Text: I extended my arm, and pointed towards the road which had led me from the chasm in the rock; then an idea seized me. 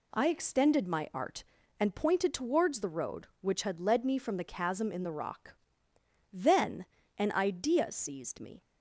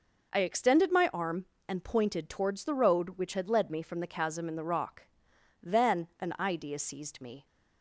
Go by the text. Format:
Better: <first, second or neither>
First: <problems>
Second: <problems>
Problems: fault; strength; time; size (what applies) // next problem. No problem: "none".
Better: second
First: says "art" for "arm"; at 1.1 s // pauses between "then" and "an"; slight; at 6.8 s; 0.32 s long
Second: none